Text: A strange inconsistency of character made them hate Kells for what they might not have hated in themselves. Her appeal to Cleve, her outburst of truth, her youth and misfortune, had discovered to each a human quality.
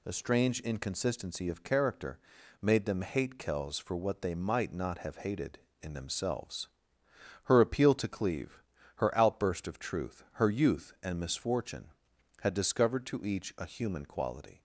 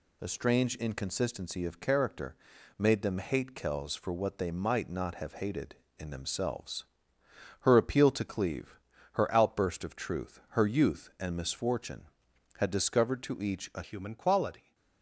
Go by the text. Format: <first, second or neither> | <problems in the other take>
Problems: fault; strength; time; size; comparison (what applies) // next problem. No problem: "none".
first | pauses between "character" and "made"; at 2.3 s; 0.42 s long; also in the first // changes voice at "human"; from 13.8 s on; 0.9 s long